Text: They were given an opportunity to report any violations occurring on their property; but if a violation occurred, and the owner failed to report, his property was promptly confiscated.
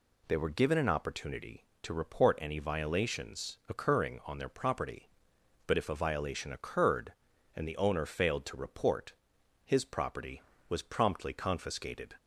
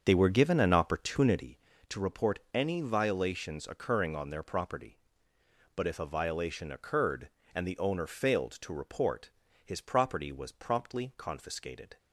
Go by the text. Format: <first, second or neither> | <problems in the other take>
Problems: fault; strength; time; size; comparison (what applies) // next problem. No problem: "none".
first | starts louder than the rest; until 1.6 s; 7 dB